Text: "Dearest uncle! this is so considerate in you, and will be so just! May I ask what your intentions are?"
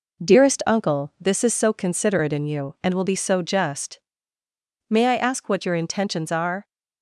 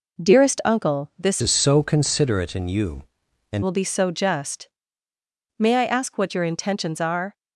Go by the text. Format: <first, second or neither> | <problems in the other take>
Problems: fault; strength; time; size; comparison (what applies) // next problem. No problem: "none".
first | changes voice from "is" to "and"; from 1.4 to 3.6 s; 2.2 s long